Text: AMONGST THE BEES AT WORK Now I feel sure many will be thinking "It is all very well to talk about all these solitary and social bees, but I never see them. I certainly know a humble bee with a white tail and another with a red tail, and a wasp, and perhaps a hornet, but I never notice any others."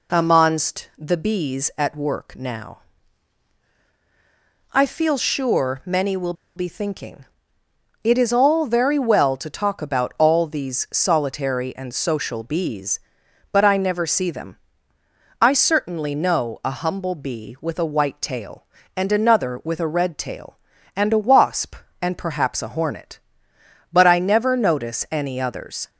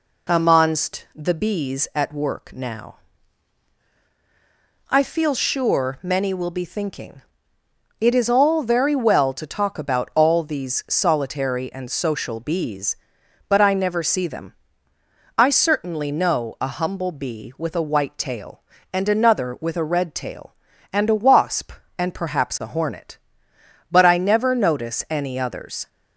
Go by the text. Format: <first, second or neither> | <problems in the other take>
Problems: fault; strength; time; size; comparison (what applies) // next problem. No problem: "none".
second | pauses between "Now" and "I"; strong; at 2.7 s; 1.9 s long; strong in the second // pauses between "will" and "be"; slight; at 6.3 s; 0.23 s long // pauses between "thinking" and "It"; noticeable; at 7.2 s; 0.76 s long; noticeable in the second